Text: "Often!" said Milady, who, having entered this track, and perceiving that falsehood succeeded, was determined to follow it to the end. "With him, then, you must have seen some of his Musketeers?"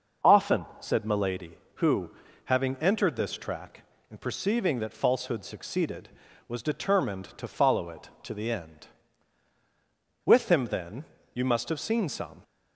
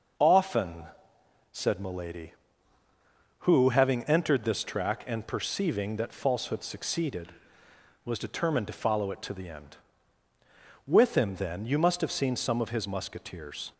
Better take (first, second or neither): second